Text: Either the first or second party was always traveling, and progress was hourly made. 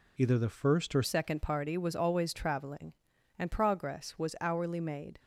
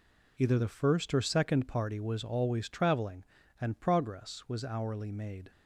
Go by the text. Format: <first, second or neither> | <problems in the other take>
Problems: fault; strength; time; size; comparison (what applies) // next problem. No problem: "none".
second | changes voice at "second"; from 1.0 s on; 4.1 s long